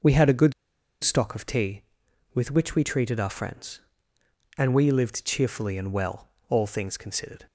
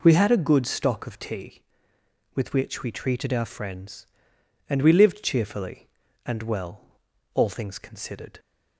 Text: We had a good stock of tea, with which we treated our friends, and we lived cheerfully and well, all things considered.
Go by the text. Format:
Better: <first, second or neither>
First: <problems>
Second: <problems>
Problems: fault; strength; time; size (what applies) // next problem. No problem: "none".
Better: second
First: pauses between "good" and "stock"; noticeable; at 0.5 s; 0.50 s long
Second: none